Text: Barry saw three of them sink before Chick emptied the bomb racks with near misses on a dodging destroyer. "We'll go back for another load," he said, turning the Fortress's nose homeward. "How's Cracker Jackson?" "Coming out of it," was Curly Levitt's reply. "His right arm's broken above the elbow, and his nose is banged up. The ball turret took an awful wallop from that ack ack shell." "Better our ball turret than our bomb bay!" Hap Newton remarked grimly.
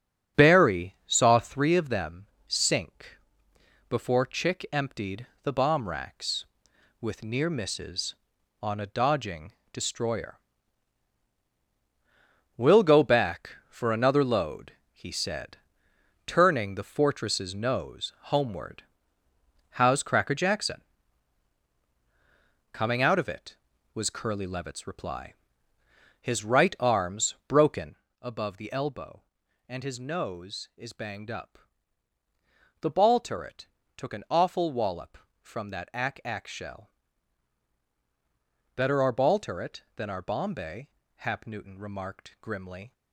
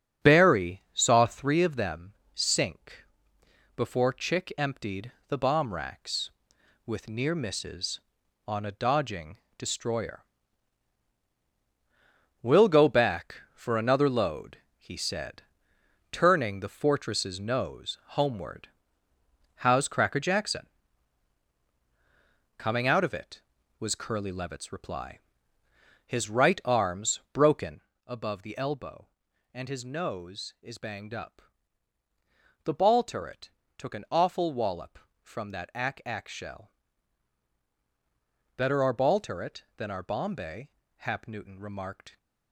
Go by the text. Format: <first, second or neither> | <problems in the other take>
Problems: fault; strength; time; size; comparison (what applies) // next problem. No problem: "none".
first | starts louder than the rest; strong; until 1.3 s; 7.5 dB; strong in the first // pauses between "them" and "sink"; slight; at 2.1 s; 0.20 s long; slight in the first // pauses between "sink" and "before"; noticeable; at 3.0 s; 0.70 s long; noticeable in the first // pauses between "emptied" and "the"; slight; at 5.1 s; 0.18 s long; slight in the first // pauses between "dodging" and "destroyer"; slight; at 9.3 s; 0.18 s long; slight in the first // pauses between "broken" and "above"; slight; at 27.8 s; 0.26 s long; slight in the first // pauses between "turret" and "took"; slight; at 33.4 s; 0.28 s long; slight in the first // stops before "grimly"; at 42.1 s